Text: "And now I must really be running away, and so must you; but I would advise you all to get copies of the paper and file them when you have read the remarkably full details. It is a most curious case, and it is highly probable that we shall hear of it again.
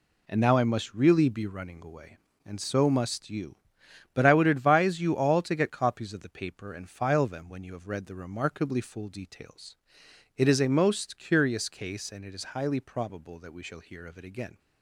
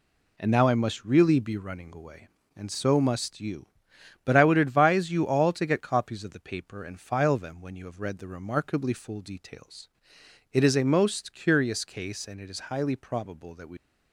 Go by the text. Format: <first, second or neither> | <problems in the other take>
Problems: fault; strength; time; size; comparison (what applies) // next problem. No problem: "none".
first | stops before "shall hear of it again"; at 13.7 s